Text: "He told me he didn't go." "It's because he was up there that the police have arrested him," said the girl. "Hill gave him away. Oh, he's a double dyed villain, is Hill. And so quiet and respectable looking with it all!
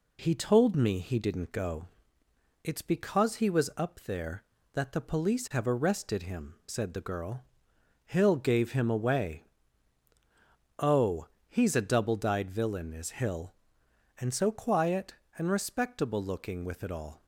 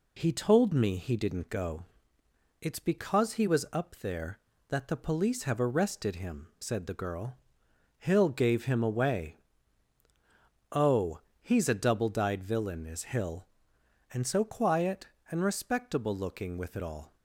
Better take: neither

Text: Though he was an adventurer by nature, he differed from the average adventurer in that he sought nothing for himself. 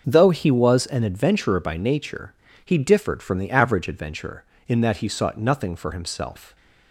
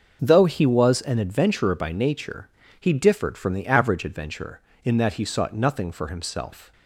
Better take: neither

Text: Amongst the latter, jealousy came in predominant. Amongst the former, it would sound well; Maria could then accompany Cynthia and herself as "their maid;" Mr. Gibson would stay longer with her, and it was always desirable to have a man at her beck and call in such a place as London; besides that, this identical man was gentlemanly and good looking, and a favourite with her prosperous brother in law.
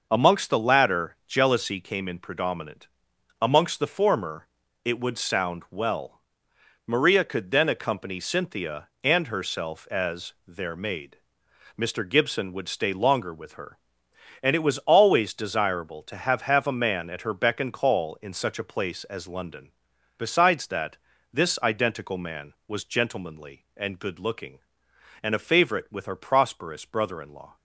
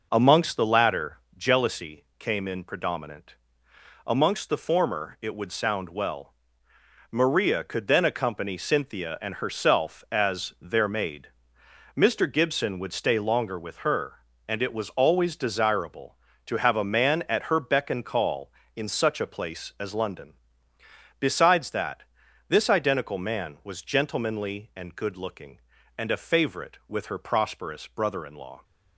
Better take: second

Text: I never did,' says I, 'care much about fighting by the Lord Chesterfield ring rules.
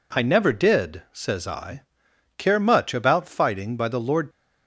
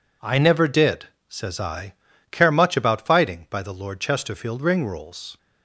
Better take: second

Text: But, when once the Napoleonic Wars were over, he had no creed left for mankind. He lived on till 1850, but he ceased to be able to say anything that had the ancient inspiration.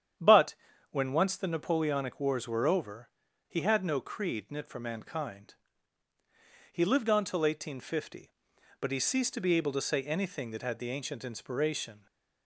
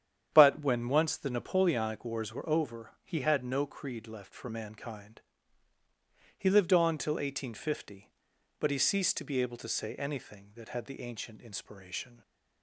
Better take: second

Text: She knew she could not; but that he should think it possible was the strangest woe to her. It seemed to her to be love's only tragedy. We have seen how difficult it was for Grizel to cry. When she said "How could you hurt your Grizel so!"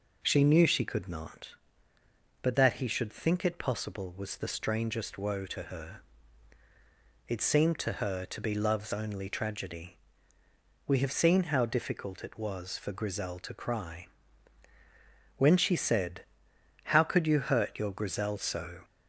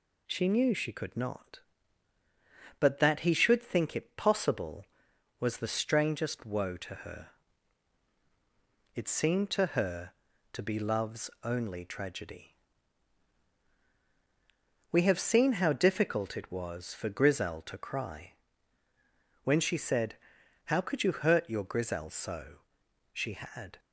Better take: first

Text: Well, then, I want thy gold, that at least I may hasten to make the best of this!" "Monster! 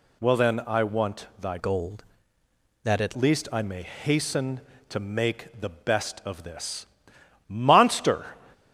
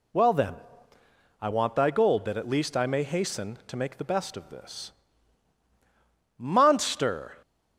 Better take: second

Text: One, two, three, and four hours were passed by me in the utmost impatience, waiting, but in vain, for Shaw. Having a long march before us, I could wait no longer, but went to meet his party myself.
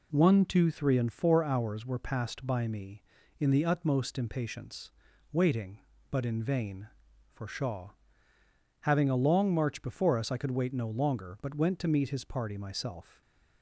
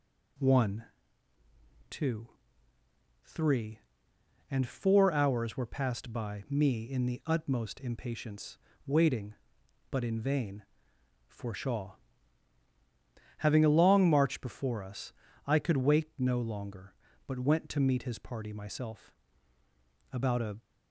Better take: first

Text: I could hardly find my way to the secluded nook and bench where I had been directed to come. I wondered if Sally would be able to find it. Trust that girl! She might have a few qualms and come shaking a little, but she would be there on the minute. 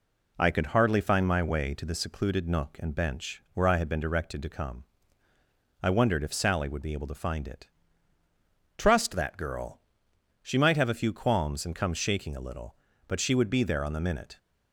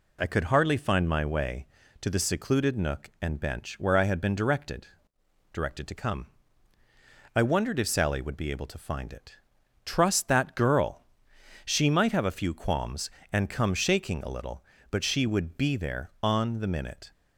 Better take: first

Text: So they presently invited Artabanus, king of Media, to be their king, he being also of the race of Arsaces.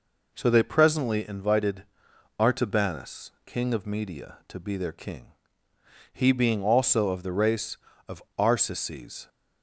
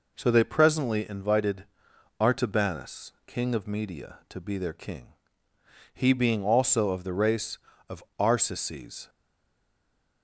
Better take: first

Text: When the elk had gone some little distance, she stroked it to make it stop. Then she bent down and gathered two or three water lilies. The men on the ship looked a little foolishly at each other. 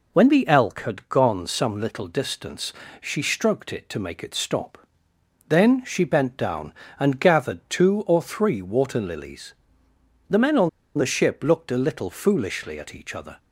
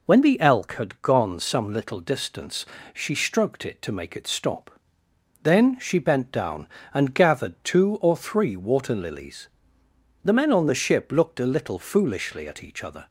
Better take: second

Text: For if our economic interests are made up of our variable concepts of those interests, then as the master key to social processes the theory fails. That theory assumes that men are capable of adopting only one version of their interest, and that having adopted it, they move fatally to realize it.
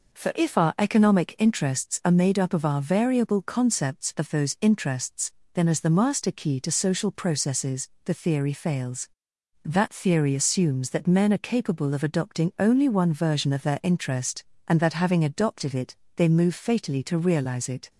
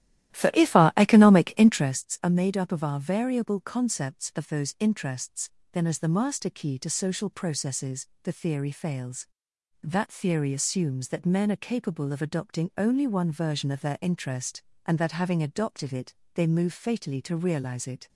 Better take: first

